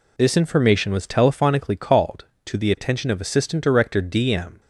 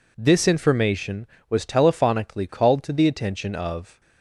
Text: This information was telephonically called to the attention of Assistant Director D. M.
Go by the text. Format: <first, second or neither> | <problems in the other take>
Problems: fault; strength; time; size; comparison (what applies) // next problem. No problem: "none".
first | stops before "Assistant Director D M"; at 3.9 s